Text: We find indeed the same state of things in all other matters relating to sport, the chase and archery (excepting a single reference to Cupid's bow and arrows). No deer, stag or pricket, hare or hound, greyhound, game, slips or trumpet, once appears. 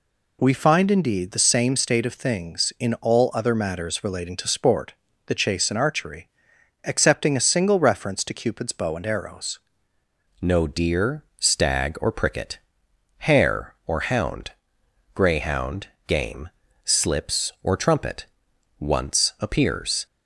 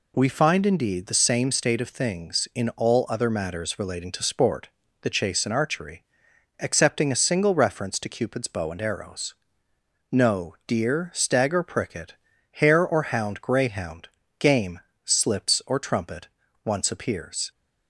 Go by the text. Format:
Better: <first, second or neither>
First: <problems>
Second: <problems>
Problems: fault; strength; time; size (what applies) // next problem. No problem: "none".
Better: second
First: changes voice at "No"; from 10.3 s on; 9.7 s long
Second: none